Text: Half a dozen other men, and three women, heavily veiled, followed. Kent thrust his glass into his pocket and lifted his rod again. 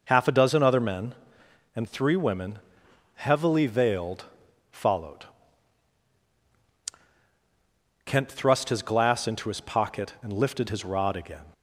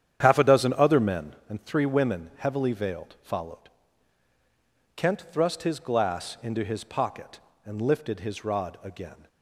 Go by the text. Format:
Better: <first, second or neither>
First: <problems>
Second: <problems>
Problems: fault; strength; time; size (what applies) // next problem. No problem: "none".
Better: first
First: none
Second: starts louder than the rest; strong; until 1.3 s; 9.5 dB